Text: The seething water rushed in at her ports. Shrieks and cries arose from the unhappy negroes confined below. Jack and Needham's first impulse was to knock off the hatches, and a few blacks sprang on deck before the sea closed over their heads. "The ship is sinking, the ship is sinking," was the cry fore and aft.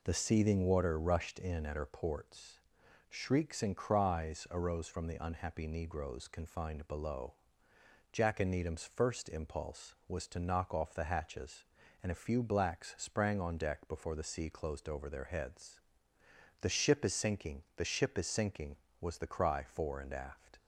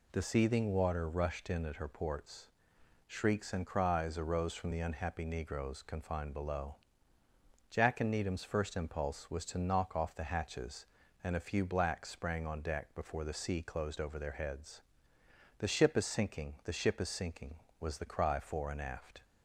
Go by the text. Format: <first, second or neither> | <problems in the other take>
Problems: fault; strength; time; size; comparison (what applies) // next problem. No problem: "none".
neither | none